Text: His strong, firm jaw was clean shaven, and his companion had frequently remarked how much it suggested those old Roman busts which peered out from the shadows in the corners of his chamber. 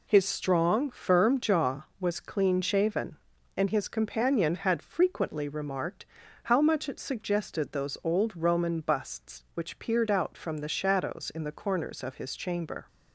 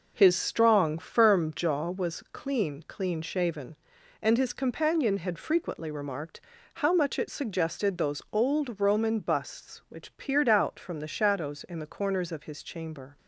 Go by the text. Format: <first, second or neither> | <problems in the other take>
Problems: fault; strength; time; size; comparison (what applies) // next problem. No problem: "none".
first | says "clean" twice; at 2.8 s // pauses between "remarked" and "how"; slight; at 6.3 s; 0.36 s long; also in the first